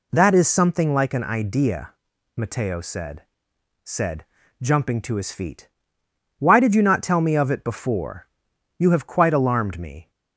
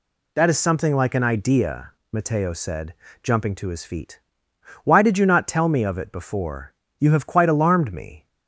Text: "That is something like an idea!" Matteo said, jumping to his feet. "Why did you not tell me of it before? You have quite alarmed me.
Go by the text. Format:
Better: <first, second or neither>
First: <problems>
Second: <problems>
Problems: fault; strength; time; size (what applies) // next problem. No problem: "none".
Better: second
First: says "said" twice; at 3.8 s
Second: none